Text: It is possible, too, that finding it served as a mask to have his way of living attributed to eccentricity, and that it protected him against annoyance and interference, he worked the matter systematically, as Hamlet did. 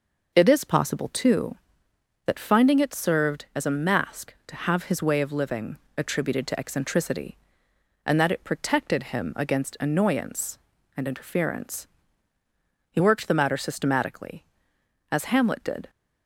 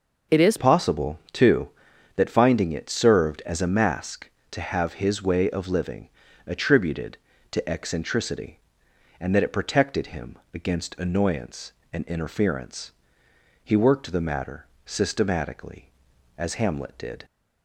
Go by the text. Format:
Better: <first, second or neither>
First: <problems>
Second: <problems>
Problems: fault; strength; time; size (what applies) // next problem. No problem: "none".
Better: first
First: pauses between "living" and "attributed"; slight; at 5.7 s; 0.18 s long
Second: changes voice at "possible"; from 0.5 s on; 16.7 s long // pauses between "living" and "attributed"; at 6.0 s; 0.40 s long // pauses between "him" and "against"; slight; at 10.3 s; 0.18 s long // pauses between "matter" and "systematically"; slight; at 14.6 s; 0.20 s long